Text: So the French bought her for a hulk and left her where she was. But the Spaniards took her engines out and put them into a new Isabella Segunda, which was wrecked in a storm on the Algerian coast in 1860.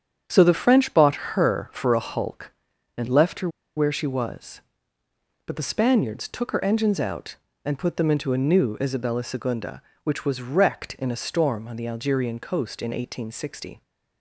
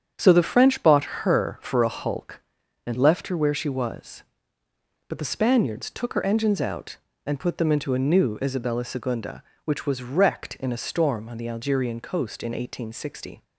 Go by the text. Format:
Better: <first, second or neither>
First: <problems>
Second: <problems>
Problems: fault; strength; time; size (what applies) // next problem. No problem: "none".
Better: second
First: starts louder than the rest; strong; until 1.2 s; 8.5 dB // pauses between "her" and "where"; slight; at 3.4 s; 0.28 s long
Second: starts louder than the rest; strong; until 1.1 s; 8.5 dB